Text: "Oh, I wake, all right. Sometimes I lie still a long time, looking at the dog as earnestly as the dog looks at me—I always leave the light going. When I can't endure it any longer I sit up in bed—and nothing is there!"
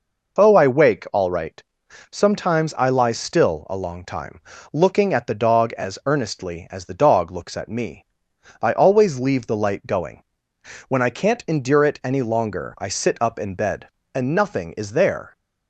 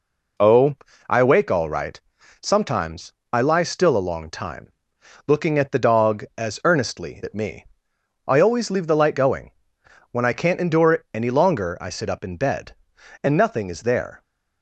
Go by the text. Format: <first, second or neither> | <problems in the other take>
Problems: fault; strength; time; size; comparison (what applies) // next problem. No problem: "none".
first | pauses between "Sometimes" and "I"; slight; at 3.1 s; 0.22 s long // skips "as the dog looks"; at 7.2 s